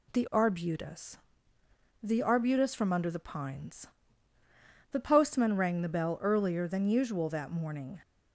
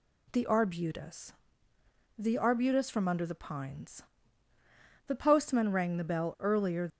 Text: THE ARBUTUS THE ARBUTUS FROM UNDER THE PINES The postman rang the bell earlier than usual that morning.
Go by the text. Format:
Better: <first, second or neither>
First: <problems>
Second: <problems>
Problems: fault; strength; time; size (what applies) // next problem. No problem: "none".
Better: first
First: pauses between "ARBUTUS" and "THE"; noticeable; at 1.1 s; 0.86 s long // pauses between "PINES" and "The"; at 3.8 s; 1.0 s long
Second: pauses between "ARBUTUS" and "THE"; noticeable; at 1.3 s; 0.86 s long // pauses between "PINES" and "The"; at 4.0 s; 1.0 s long // stops before "than usual that morning"; at 6.8 s